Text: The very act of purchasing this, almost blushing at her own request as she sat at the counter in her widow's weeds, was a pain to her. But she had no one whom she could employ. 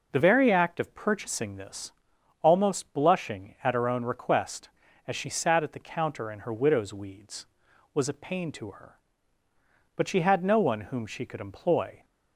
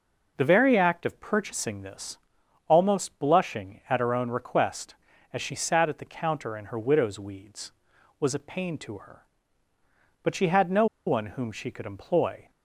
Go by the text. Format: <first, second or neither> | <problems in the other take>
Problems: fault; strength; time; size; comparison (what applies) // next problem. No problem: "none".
first | pauses between "no" and "one"; slight; at 10.8 s; 0.21 s long